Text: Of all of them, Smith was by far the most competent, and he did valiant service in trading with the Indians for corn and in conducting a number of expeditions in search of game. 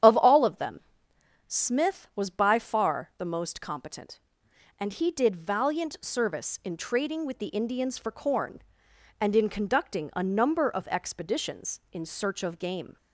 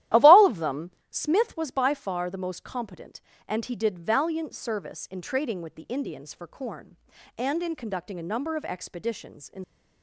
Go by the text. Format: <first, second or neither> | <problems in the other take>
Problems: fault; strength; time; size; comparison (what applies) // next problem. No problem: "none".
first | starts louder than the rest; strong; until 1.3 s; 13.5 dB; strong in the first // stops before "search of game"; at 9.6 s